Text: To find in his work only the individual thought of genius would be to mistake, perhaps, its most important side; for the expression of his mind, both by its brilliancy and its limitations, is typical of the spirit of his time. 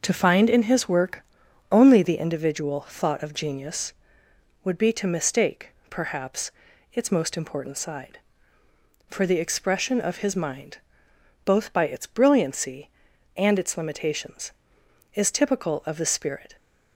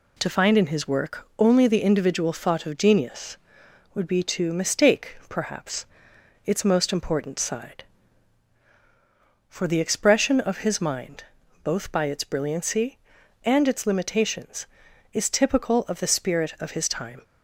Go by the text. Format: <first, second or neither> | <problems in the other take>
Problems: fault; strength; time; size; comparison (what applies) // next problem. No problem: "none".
second | starts louder than the rest; until 1.0 s; 6 dB // pauses between "work" and "only"; noticeable; at 1.2 s; 0.48 s long // stops before "of his time"; at 16.5 s